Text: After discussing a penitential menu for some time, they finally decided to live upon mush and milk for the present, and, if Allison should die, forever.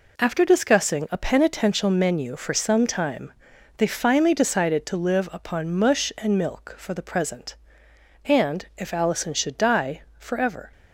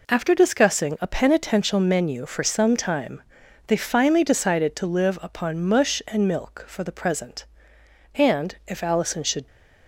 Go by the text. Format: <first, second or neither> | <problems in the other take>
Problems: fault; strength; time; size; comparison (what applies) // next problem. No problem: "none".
first | stops before "die forever"; at 9.4 s